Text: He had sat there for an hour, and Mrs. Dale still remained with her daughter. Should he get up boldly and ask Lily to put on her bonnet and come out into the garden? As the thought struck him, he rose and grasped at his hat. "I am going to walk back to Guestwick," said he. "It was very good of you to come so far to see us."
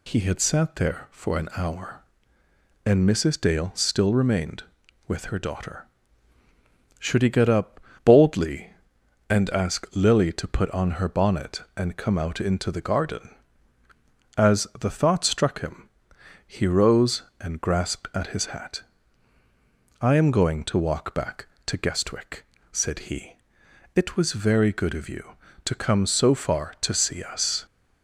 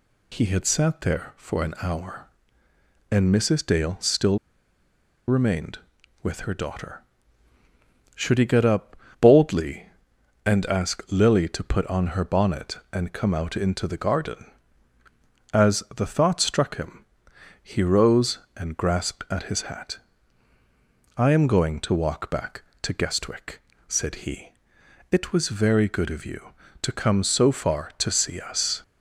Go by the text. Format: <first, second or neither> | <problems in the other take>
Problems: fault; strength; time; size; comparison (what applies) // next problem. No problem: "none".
first | pauses between "still" and "remained"; noticeable; at 4.3 s; 0.90 s long // pauses between "up" and "boldly"; slight; at 8.9 s; 0.24 s long; slight in the first